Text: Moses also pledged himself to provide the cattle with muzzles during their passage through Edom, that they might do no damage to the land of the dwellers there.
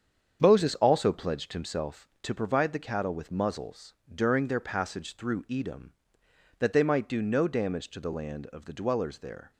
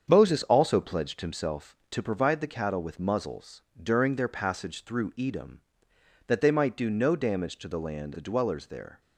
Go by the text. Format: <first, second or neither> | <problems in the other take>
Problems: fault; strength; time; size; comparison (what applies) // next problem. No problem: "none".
first | starts louder than the rest; strong; until 1.1 s; 7.5 dB; strong in the first // pauses between "muzzles" and "during"; slight; at 3.6 s; 0.20 s long; slight in the first // skips "of"; at 8.1 s